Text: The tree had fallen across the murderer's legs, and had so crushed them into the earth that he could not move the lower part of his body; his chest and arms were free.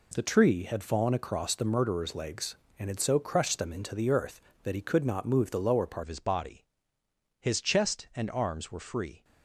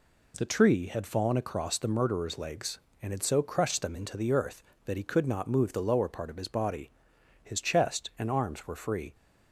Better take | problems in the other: second | changes voice at "of"; from 6.0 s on; 3.2 s long

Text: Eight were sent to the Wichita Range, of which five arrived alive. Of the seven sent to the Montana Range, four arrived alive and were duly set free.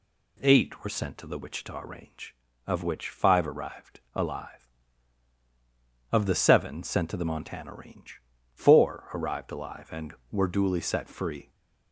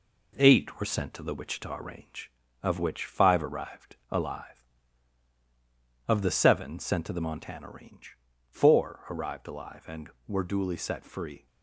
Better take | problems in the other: first | gets quieter; throughout; 3.5 dB

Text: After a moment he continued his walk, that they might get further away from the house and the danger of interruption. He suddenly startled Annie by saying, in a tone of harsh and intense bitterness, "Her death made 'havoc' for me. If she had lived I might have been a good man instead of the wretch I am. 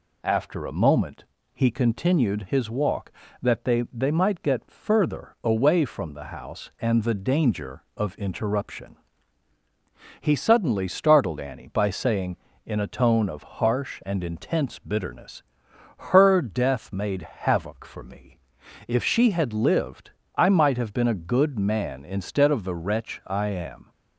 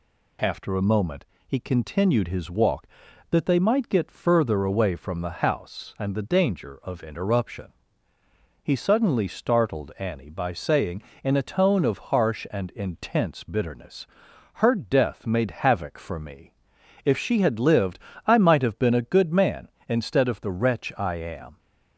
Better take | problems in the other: second | pauses between "moment" and "he"; slight; at 1.2 s; 0.28 s long; slight in the second // says "they" twice; at 3.9 s // pauses between "lived" and "I"; slight; at 20.1 s; 0.26 s long; slight in the second

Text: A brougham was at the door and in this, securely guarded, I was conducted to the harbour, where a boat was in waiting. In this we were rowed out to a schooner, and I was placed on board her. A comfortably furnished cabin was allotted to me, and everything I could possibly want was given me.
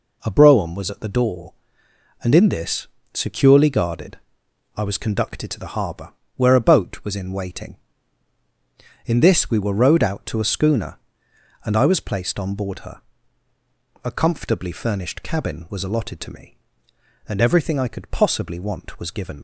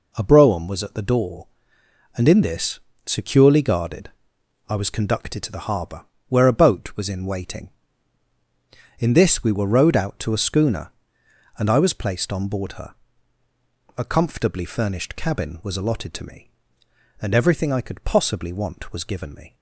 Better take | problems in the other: second | stops before "me"; at 19.3 s

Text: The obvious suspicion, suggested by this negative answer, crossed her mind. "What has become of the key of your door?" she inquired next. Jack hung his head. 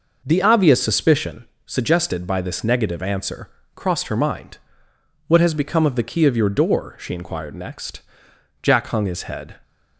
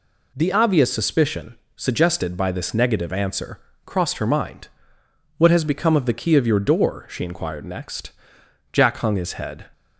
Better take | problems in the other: second | starts louder than the rest; noticeable; until 1.4 s; 5.5 dB

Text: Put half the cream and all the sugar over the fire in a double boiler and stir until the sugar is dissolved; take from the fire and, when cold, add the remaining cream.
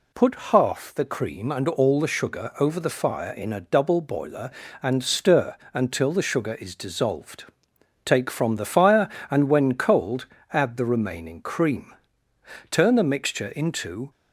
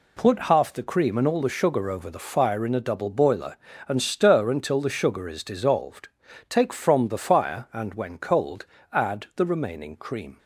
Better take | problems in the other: second | pauses between "stir" and "until"; slight; at 5.5 s; 0.16 s long // goes on to say "Turn the mixture into"; from 12.7 s on; 1.4 s long

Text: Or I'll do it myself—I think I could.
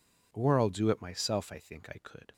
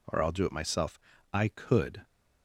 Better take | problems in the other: first | skips "think I"; at 1.4 s

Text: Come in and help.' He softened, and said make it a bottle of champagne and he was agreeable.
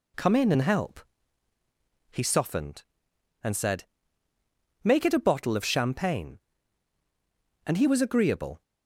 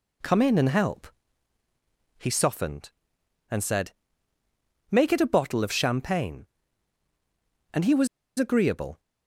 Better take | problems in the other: first | pauses between "said" and "make"; noticeable; at 3.9 s; 0.98 s long; noticeable in the first // pauses between "was" and "agreeable"; slight; at 8.0 s; 0.30 s long

